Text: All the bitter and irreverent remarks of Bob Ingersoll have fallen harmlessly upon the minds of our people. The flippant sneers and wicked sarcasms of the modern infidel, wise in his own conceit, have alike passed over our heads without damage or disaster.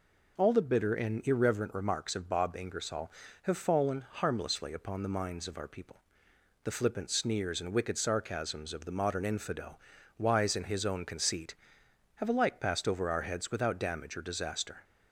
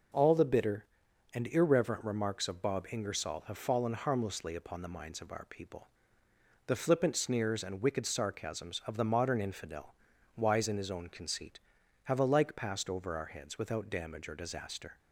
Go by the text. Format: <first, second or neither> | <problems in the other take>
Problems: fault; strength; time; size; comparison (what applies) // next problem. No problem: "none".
neither | none